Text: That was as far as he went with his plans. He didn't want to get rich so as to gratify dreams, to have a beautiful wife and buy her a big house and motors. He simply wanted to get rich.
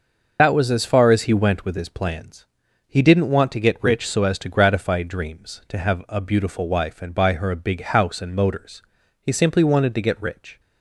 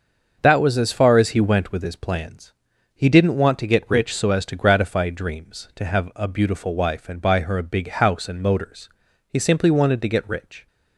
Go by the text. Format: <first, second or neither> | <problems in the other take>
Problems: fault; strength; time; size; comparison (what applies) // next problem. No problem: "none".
second | loses the start of "That"; at 0.3 s; 65 ms // starts louder than the rest; noticeable; until 1.4 s; 6 dB; also in the second